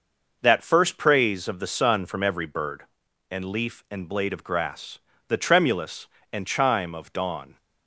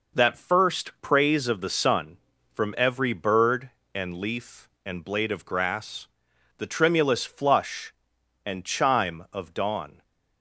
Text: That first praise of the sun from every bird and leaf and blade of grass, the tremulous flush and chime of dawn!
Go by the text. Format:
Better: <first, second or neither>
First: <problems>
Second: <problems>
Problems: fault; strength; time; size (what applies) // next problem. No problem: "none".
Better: second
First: skips "flush"; at 6.1 s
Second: none